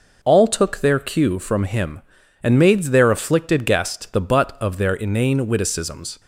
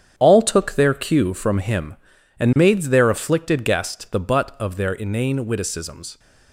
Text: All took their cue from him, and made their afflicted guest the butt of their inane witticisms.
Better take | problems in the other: first | gets quieter; strong; throughout; 9.5 dB

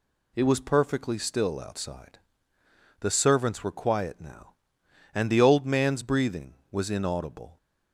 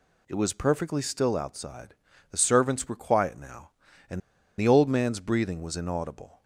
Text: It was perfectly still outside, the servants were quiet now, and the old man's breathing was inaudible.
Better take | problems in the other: first | pauses between "and" and "the"; at 4.2 s; 0.38 s long

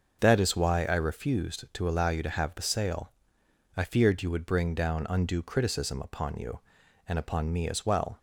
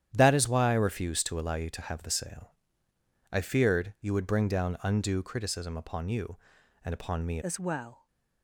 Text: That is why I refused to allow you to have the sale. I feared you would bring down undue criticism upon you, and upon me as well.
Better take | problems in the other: first | starts louder than the rest; strong; until 1.1 s; 10 dB; noticeable in the first // changes voice at "as"; from 7.4 s on; 0.6 s long

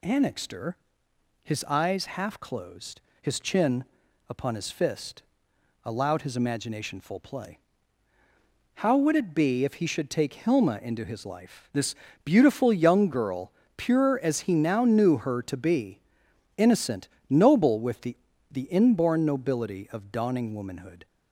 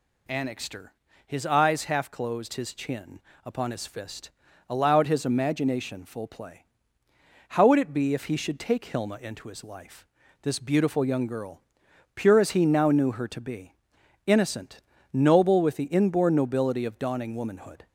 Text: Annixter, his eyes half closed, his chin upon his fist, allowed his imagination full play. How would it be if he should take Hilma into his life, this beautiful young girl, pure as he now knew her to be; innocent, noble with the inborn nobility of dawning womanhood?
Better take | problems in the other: second | pauses between "chin" and "upon"; at 3.8 s; 0.44 s long; slight in the second // pauses between "this" and "beautiful"; slight; at 11.9 s; 0.30 s long // says "the" twice; at 18.4 s

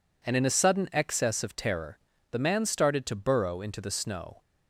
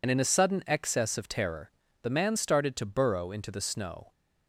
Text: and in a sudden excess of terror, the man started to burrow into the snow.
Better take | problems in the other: first | loses the start of "and"; at 0.0 s; 55 ms

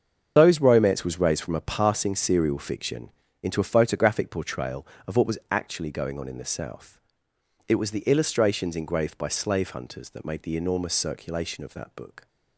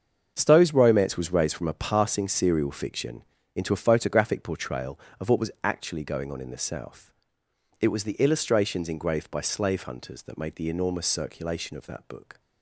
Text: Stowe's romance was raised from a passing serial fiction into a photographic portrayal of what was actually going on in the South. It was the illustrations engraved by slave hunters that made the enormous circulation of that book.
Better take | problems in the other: second | loses the start of "Stowe's"; at 0.3 s; 130 ms // starts louder than the rest; until 1.3 s; 7 dB; also in the second // pauses between "fiction" and "into"; slight; at 3.1 s; 0.32 s long; slight in the second

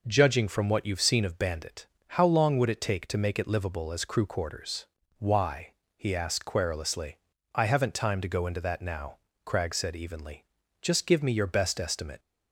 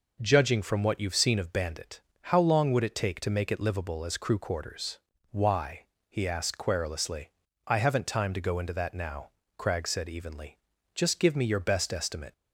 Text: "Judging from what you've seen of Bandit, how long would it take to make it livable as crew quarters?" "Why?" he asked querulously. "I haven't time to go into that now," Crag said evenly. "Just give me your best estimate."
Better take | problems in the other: neither | none

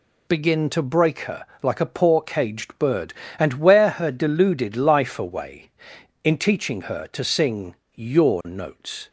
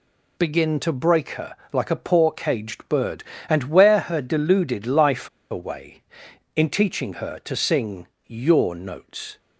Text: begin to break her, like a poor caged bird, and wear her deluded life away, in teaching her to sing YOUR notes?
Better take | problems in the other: first | pauses between "life" and "away"; slight; at 5.2 s; 0.22 s long // pauses between "sing" and "YOUR"; slight; at 8.0 s; 0.20 s long; slight in the first

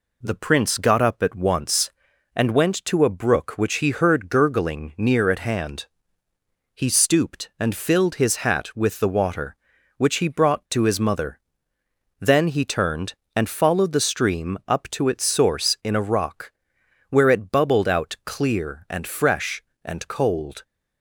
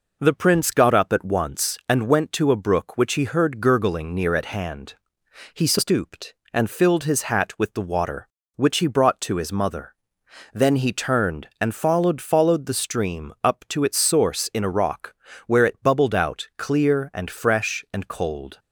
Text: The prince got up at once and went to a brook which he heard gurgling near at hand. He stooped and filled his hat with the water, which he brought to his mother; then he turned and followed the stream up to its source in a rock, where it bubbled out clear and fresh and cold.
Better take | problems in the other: first | says "followed" twice; at 12.2 s

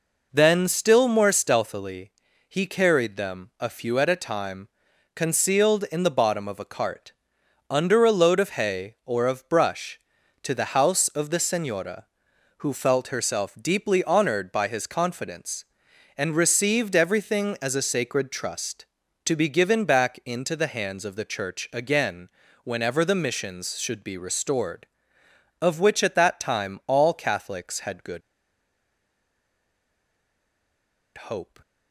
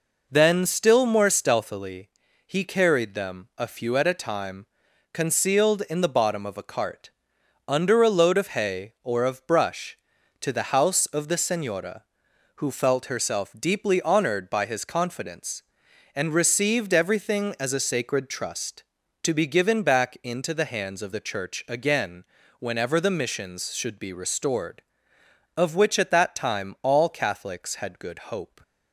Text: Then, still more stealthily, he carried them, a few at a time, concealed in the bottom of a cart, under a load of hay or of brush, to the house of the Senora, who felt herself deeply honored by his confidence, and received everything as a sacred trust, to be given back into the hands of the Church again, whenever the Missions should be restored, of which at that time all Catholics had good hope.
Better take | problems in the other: second | pauses between "good" and "hope"; strong; at 28.2 s; 2.9 s long

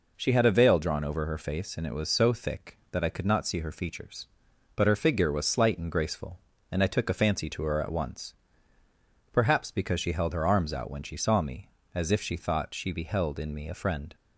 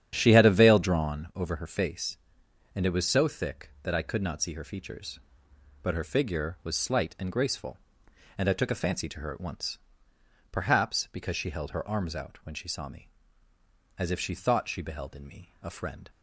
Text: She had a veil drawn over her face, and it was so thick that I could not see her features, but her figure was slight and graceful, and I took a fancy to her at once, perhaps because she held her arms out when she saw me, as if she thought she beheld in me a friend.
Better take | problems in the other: first | starts louder than the rest; strong; until 1.3 s; 9.5 dB

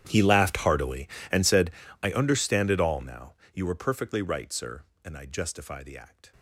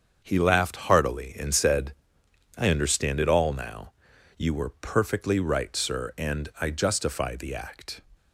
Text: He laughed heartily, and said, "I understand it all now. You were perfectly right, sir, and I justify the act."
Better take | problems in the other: second | gets quieter; strong; throughout; 23 dB // starts louder than the rest; strong; until 1.0 s; 10.5 dB; also in the second

